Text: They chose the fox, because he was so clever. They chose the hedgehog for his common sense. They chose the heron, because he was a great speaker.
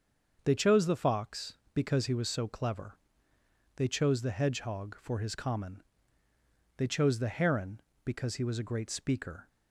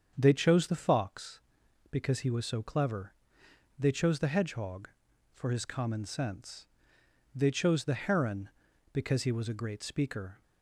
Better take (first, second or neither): second